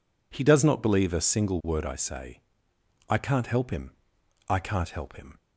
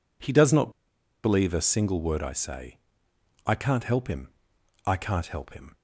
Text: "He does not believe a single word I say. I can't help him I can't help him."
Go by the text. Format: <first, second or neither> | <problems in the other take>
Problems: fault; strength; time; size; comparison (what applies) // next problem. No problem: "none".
first | pauses between "not" and "believe"; noticeable; at 0.6 s; 0.54 s long // pauses between "him" and "I"; noticeable; at 4.2 s; 0.58 s long; noticeable in the first